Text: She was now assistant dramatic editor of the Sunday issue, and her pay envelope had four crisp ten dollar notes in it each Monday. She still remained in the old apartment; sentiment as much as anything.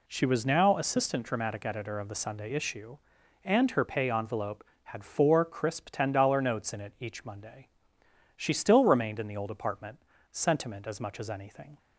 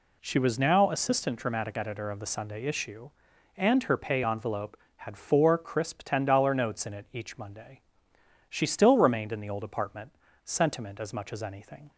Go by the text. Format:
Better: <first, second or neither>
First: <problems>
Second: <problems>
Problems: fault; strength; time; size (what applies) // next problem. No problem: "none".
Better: neither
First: none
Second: none